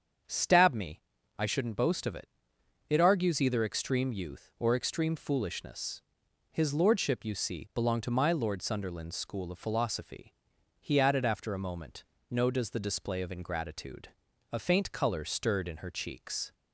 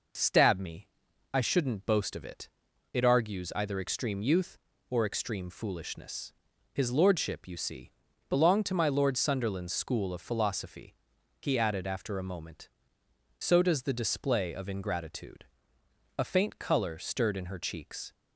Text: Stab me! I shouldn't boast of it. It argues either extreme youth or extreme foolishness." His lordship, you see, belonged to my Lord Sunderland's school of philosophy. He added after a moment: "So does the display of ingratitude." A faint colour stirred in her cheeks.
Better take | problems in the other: second | starts louder than the rest; strong; until 1.6 s; 7 dB // says "No" for "So"; at 12.3 s

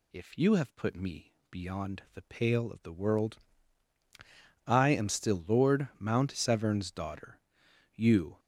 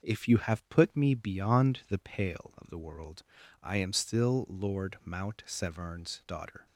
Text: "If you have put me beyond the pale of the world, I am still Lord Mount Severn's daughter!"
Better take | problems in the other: second | pauses between "me" and "beyond"; slight; at 1.3 s; 0.20 s long // goes on to say "You"; slight; from 7.9 s on; 0.44 s long

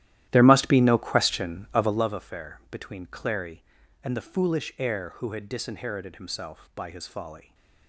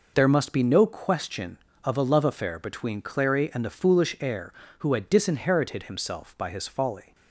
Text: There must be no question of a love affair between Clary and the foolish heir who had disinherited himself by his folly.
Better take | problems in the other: second | starts louder than the rest; strong; until 2.1 s; 13.5 dB

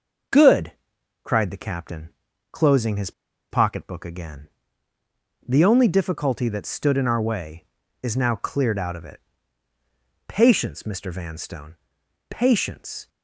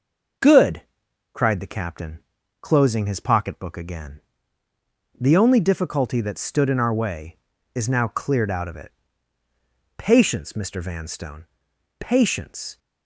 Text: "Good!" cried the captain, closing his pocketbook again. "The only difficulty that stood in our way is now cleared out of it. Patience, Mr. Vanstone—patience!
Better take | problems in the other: second | pauses between "his" and "pocketbook"; at 3.1 s; 0.40 s long

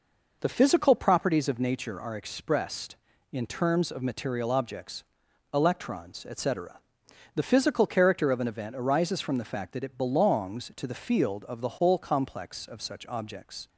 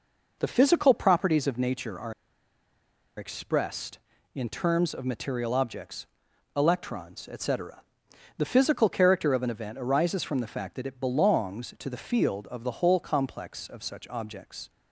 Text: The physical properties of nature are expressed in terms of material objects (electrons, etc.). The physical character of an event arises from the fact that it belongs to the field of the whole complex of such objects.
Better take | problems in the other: first | pauses between "are" and "expressed"; at 2.1 s; 1.0 s long

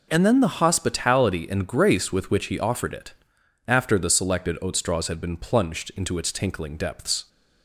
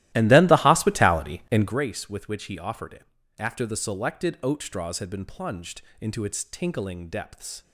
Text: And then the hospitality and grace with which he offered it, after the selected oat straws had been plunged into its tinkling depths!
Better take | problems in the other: first | starts louder than the rest; strong; until 1.8 s; 15.5 dB // pauses between "plunged" and "into"; slight; at 5.8 s; 0.20 s long

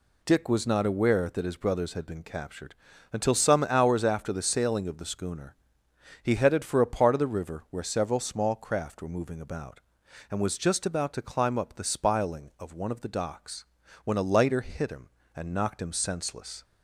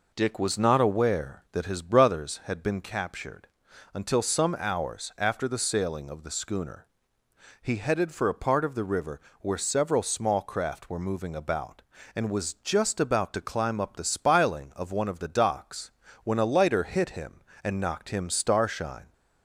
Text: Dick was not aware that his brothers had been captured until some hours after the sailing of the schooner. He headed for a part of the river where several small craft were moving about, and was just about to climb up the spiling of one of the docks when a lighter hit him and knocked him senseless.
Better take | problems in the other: first | pauses between "captured" and "until"; noticeable; at 3.4 s; 0.48 s long; also in the first // pauses between "river" and "where"; slight; at 9.2 s; 0.20 s long // pauses between "docks" and "when"; slight; at 15.9 s; 0.34 s long; also in the first // says "starshine" for "senseless"; at 18.2 s

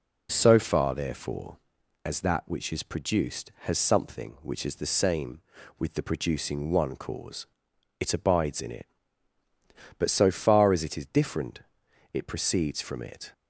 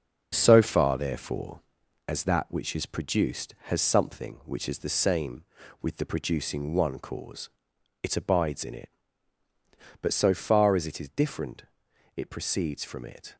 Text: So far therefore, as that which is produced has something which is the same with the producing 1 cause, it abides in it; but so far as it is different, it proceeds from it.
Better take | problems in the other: first | gets quieter; throughout; 6.5 dB

